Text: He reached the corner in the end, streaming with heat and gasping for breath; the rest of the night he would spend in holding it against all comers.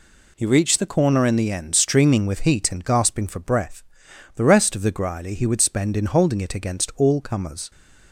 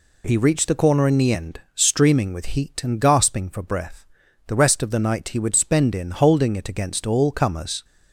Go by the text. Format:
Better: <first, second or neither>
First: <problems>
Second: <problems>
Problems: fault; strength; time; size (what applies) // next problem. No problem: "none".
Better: second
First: says "grily" for "night"; at 4.9 s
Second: none